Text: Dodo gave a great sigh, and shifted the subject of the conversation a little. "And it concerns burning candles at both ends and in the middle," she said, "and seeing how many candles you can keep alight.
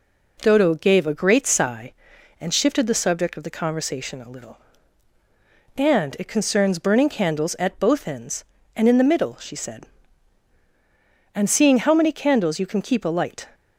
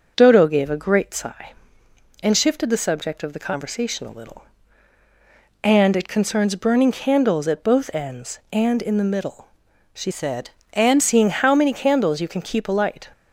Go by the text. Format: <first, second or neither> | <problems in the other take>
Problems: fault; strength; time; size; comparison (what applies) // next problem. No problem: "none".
first | starts louder than the rest; until 1.1 s; 6.5 dB // changes voice from "said" to "and"; from 10.1 to 11.0 s; 0.9 s long